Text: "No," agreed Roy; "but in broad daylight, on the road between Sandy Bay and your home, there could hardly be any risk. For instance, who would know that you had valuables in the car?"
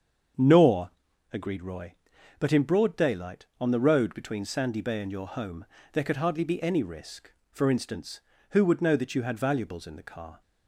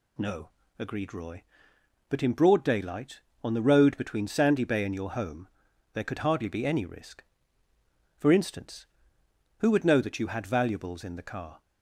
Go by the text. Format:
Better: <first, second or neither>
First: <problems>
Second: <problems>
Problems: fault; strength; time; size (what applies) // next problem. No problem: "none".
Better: second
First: starts louder than the rest; strong; until 1.7 s; 7 dB // says "Nor" for "No"; at 0.3 s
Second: none